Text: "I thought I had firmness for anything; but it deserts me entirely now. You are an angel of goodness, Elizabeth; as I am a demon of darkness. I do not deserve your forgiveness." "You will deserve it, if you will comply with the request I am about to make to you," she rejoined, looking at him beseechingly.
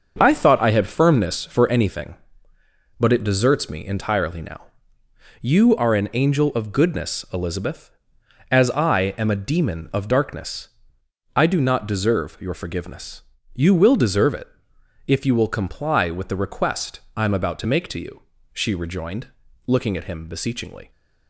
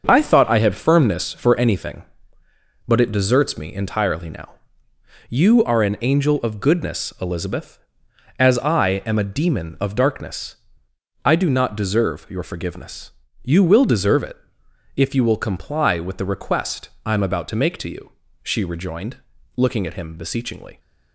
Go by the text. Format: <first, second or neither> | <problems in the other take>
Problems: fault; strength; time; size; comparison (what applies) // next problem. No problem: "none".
neither | starts louder than the rest; the same in both // pauses between "request" and "I"; slight; the same in both